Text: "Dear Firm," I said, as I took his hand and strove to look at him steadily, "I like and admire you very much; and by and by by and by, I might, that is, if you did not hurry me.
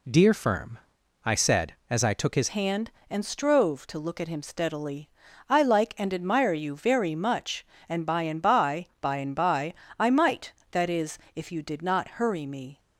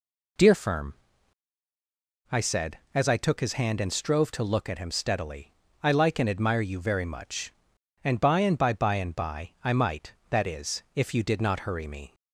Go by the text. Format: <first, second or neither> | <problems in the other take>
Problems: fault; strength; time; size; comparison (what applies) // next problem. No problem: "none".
second | changes voice at "hand"; from 2.4 s on; 10.3 s long